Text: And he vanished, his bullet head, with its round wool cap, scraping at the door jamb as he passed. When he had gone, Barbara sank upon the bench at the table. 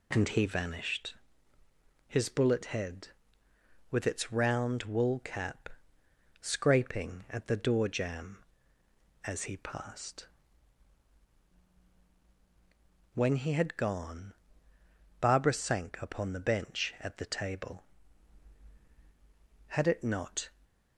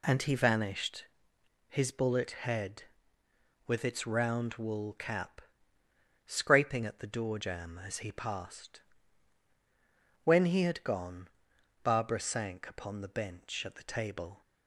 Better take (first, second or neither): second